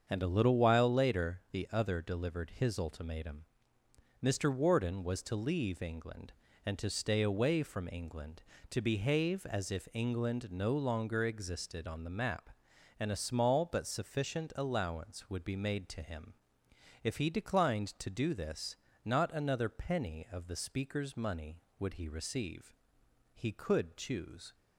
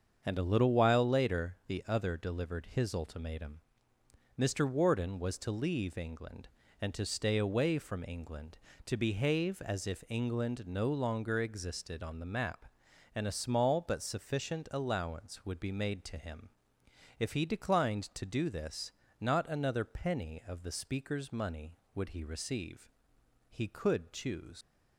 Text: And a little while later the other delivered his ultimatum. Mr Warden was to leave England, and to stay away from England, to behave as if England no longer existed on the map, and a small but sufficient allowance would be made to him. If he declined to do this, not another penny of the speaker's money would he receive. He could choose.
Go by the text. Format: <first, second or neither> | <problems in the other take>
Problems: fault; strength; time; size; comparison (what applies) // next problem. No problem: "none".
first | starts louder than the rest; strong; until 1.2 s; 7 dB; strong in the first // leaves "choose" unfinished; at 24.6 s; 85 ms